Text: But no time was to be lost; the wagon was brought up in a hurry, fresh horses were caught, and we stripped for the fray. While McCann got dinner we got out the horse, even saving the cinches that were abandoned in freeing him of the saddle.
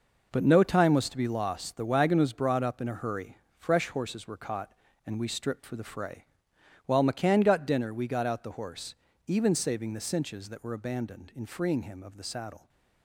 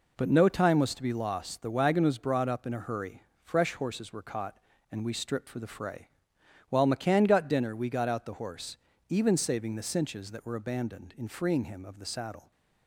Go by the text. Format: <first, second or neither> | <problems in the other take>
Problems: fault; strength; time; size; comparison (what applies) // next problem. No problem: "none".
second | gets quieter; strong; throughout; 9.5 dB